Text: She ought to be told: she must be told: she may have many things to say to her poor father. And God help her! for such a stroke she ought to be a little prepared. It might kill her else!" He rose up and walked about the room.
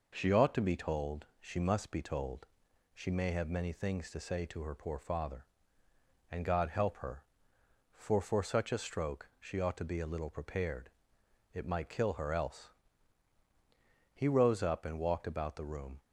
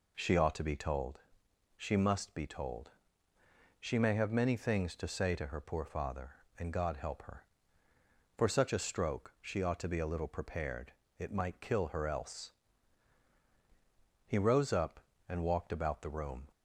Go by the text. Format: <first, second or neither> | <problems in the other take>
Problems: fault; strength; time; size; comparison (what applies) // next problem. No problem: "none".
second | says "for" twice; at 8.2 s